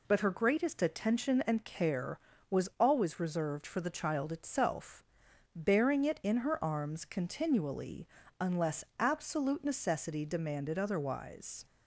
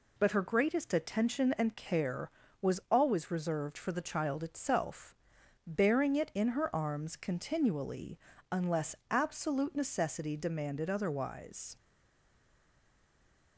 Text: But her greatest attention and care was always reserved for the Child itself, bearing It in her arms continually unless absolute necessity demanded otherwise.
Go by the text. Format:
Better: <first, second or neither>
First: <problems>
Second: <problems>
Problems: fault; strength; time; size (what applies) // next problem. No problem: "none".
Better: first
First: pauses between "continually" and "unless"; slight; at 8.0 s; 0.34 s long // pauses between "unless" and "absolute"; slight; at 8.8 s; 0.16 s long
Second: pauses between "continually" and "unless"; slight; at 8.1 s; 0.34 s long // pauses between "unless" and "absolute"; slight; at 8.9 s; 0.16 s long // stays silent after the last word; noticeable; from 11.7 s on; 1.8 s long